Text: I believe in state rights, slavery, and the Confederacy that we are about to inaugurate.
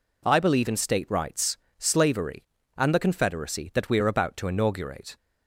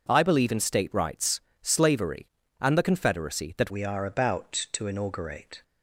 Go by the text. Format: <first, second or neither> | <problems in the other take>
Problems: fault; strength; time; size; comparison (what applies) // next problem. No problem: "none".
first | changes voice at "we"; from 3.7 s on; 1.9 s long